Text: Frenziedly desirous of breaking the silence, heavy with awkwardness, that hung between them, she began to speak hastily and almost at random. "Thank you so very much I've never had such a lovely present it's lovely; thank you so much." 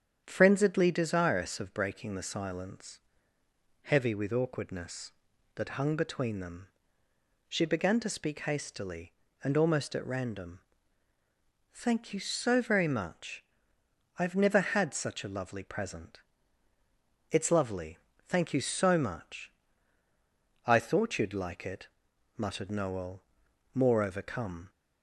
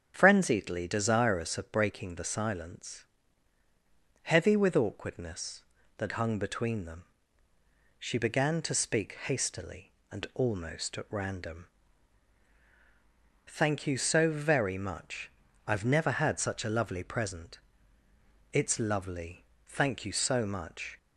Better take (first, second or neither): second